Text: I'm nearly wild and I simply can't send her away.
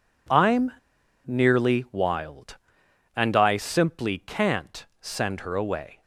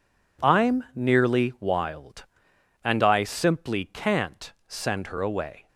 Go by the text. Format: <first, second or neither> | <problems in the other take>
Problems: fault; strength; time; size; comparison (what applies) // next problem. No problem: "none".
second | pauses between "I'm" and "nearly"; noticeable; at 0.7 s; 0.56 s long // pauses between "can't" and "send"; slight; at 4.8 s; 0.16 s long; slight in the second